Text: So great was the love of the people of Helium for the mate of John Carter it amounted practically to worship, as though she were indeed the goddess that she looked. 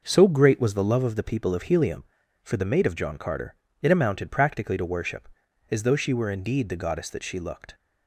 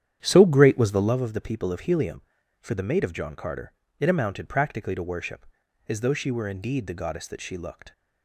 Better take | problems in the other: first | starts louder than the rest; strong; until 1.1 s; 10 dB // pauses between "Carter" and "it"; slight; at 3.7 s; 0.26 s long; slight in the first

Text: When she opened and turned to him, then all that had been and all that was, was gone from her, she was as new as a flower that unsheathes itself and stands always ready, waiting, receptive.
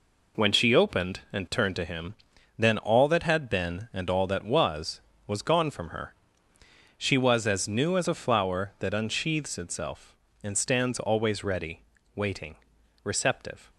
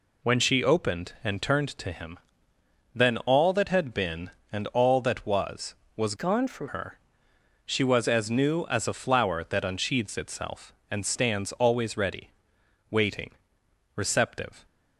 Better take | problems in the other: first | changes voice from "gone" to "from"; from 6.1 to 6.6 s; 0.5 s long

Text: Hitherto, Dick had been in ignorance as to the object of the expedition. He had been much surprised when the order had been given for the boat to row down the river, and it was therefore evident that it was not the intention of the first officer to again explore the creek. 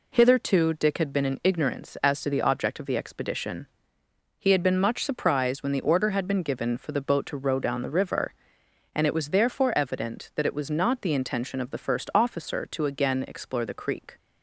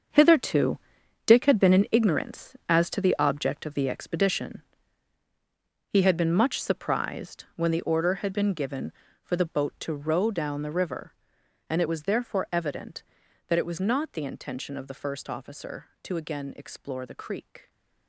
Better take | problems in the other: first | gets quieter; strong; throughout; 11.5 dB

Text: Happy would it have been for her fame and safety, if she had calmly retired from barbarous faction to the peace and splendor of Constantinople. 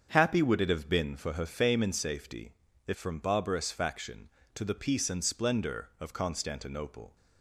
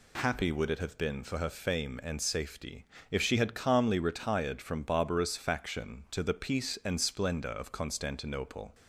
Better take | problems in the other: second | starts louder than the rest; strong; until 1.1 s; 7 dB // skips "she had calmly retired"; at 2.9 s

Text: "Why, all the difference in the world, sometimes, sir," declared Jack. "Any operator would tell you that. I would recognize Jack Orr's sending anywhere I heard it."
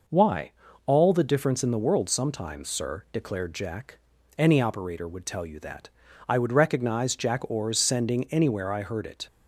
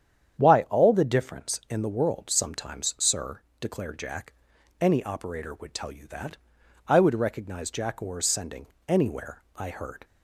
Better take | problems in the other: first | starts louder than the rest; strong; until 1.3 s; 9 dB // pauses between "sending" and "anywhere"; slight; at 8.6 s; 0.20 s long // stops before "it"; at 10.0 s

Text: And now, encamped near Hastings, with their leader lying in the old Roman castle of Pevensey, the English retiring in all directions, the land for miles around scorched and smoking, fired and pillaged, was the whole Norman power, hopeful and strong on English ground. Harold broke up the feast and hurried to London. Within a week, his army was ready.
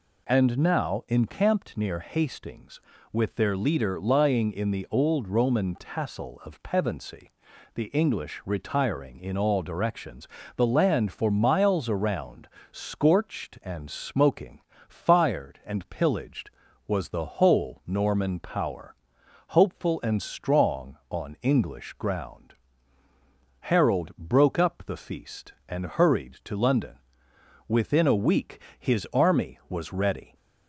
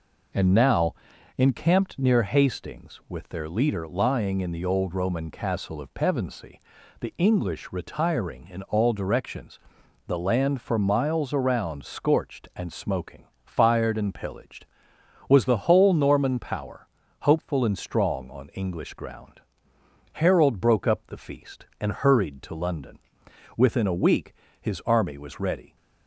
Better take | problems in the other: second | says "tassel" for "castle"; at 5.7 s // pauses between "around" and "scorched"; slight; at 12.4 s; 0.24 s long

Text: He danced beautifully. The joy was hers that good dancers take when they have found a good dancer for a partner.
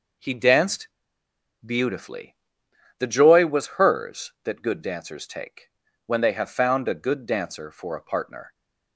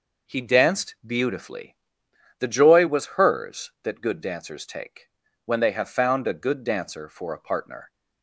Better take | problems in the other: second | pauses between "danced" and "beautifully"; noticeable; at 0.8 s; 0.74 s long // pauses between "take" and "when"; slight; at 5.6 s; 0.36 s long; slight in the second

